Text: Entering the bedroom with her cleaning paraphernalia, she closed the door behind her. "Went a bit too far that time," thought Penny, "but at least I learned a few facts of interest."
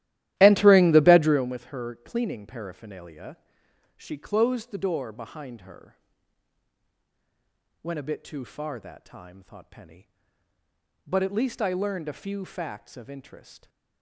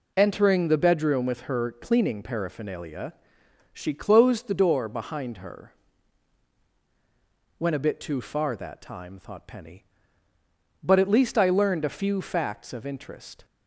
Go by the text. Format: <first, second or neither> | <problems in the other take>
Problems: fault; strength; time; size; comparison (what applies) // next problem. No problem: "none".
second | starts louder than the rest; strong; until 1.5 s; 14.5 dB